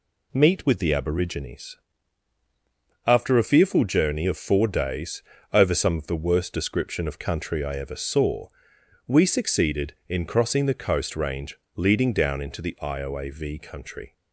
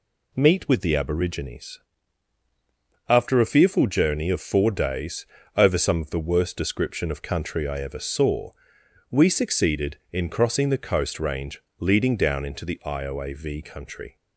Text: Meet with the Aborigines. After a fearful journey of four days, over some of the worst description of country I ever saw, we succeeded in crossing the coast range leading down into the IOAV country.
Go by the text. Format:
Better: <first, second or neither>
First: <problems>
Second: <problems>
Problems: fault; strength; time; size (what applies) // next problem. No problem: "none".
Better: neither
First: pauses between "range" and "leading"; slight; at 11.5 s; 0.18 s long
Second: pauses between "range" and "leading"; slight; at 11.6 s; 0.18 s long